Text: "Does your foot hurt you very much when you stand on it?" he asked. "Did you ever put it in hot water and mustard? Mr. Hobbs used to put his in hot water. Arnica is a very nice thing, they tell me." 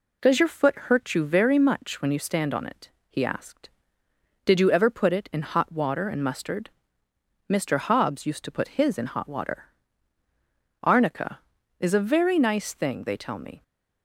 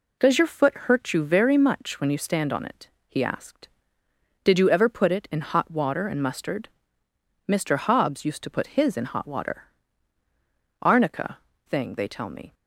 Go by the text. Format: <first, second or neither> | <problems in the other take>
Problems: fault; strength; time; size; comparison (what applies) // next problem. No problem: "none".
first | skips "is a very nice"; at 11.5 s